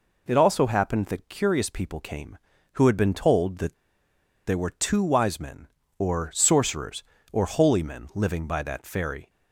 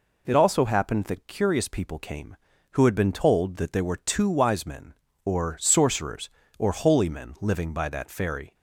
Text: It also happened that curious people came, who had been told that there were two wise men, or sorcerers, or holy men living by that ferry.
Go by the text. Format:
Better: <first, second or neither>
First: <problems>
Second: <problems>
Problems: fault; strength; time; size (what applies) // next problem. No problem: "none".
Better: second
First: pauses between "that" and "there"; noticeable; at 3.7 s; 0.73 s long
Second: none